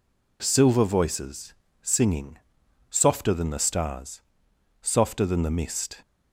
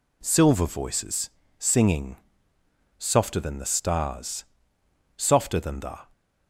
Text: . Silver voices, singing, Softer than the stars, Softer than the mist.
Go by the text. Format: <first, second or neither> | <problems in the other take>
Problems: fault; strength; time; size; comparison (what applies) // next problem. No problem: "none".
first | stops before "mist"; at 6.1 s